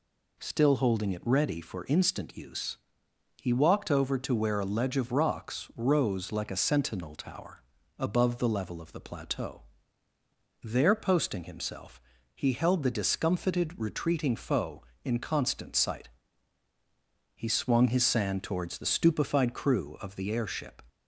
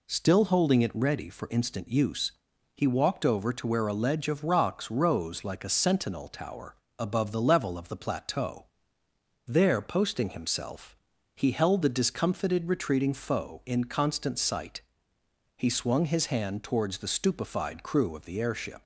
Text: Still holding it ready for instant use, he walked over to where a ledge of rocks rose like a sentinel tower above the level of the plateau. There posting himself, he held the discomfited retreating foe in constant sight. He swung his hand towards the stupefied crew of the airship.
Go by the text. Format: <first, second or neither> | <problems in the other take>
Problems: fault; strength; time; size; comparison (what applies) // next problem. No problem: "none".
second | pauses between "tower" and "above"; slight; at 7.6 s; 0.36 s long; slight in the second // says "sand" for "hand"; at 18.0 s